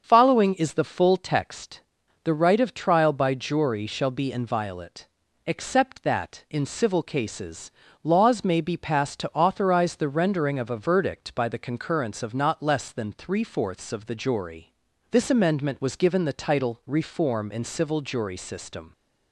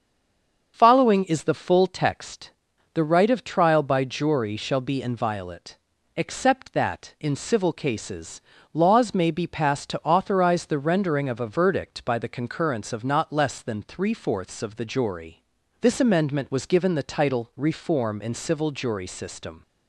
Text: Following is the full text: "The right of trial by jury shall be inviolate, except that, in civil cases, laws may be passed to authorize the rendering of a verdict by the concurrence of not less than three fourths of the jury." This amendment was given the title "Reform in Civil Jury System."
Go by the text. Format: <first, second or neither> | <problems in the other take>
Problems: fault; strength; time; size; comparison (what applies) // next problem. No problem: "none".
first | stays silent before the first word; slight; until 0.7 s; 0.7 s long // starts louder than the rest; until 1.7 s; 7 dB; also in the first